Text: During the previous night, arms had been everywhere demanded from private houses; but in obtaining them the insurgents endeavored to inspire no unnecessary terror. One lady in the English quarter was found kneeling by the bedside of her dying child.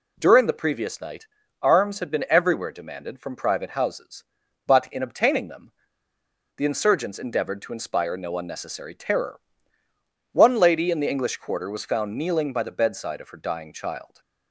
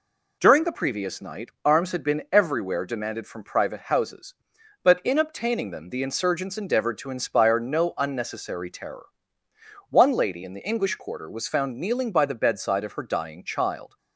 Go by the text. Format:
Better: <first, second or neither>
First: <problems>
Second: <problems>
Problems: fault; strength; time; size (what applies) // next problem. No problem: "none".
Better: second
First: pauses between "them" and "the"; noticeable; at 5.7 s; 0.86 s long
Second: none